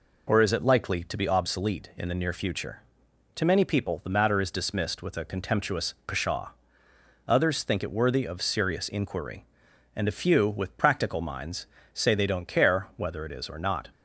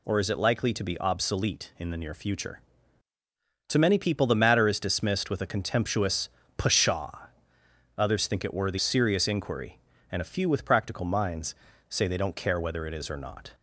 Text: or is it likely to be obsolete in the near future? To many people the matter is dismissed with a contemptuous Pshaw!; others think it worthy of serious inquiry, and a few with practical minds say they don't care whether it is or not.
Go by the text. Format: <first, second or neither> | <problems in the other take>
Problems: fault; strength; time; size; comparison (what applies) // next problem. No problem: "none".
first | pauses between "contemptuous" and "Pshaw"; slight; at 6.2 s; 0.28 s long // skips "of"; at 8.7 s // pauses between "minds" and "say"; slight; at 11.5 s; 0.36 s long; slight in the first